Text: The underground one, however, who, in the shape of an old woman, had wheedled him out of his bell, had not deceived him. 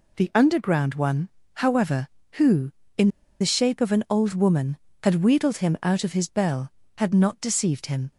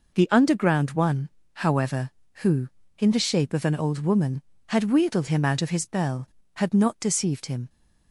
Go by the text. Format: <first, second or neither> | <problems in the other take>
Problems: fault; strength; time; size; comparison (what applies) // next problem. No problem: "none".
second | pauses between "in" and "the"; slight; at 3.0 s; 0.32 s long